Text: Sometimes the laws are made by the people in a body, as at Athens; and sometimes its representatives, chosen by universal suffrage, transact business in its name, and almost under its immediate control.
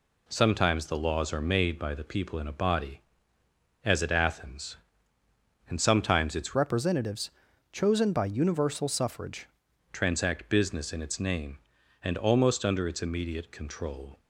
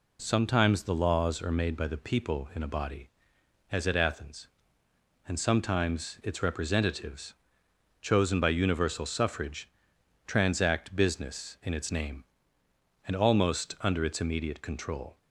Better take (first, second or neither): second